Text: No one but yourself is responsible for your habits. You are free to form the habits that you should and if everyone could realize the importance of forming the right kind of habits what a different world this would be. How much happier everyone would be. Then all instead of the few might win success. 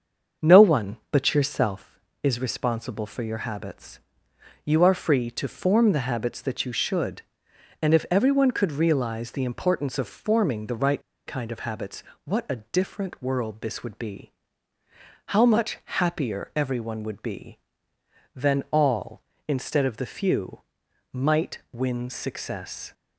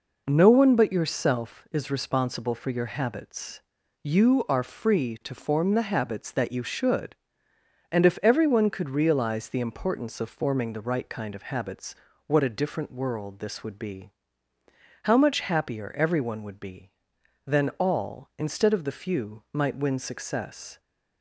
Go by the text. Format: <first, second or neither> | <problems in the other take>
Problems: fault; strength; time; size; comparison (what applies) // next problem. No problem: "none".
second | starts louder than the rest; until 1.5 s; 7 dB // pauses between "right" and "kind"; slight; at 11.0 s; 0.25 s long // pauses between "habits" and "what"; slight; at 12.0 s; 0.22 s long; slight in the second // pauses between "few" and "might"; noticeable; at 20.6 s; 0.50 s long